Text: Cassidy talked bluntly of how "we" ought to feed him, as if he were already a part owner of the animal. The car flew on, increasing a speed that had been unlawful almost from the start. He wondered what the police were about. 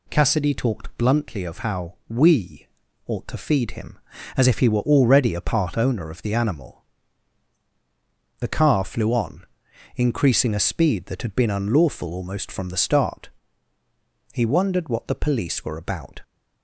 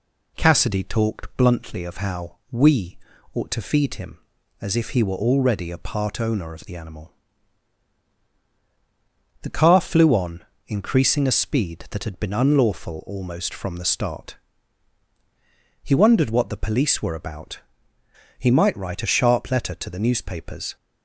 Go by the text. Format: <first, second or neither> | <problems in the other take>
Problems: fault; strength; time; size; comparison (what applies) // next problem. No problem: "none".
first | pauses between "we" and "ought"; at 2.9 s; 0.38 s long; also in the first // goes on to say "He might write a sharp letter to the newspapers"; strong; from 18.3 s on; 2.3 s long